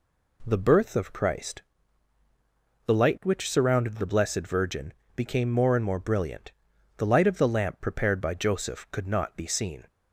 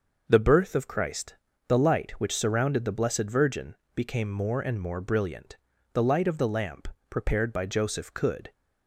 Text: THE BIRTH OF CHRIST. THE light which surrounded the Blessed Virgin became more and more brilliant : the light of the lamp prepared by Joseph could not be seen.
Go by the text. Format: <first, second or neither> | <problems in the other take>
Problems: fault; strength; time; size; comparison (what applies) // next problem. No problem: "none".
first | pauses between "Virgin" and "became"; slight; at 3.7 s; 0.22 s long; slight in the first // pauses between "lamp" and "prepared"; slight; at 6.8 s; 0.22 s long // stops before "not be seen"; at 8.5 s